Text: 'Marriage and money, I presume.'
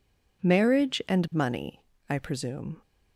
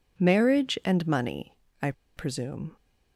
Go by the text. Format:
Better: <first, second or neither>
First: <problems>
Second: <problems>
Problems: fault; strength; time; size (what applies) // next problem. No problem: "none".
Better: first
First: none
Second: pauses between "I" and "presume"; slight; at 1.9 s; 0.24 s long